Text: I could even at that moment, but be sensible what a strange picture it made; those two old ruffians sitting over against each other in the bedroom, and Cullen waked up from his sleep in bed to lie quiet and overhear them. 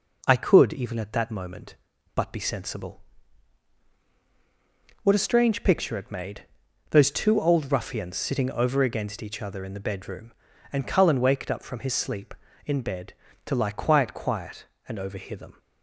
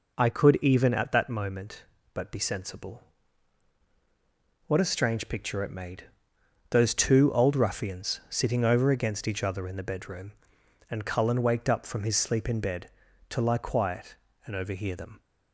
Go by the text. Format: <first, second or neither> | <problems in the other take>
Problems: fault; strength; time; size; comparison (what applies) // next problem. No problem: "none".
second | pauses between "sensible" and "what"; strong; at 3.0 s; 2.0 s long; strong in the second // says "quiet" twice; at 14.1 s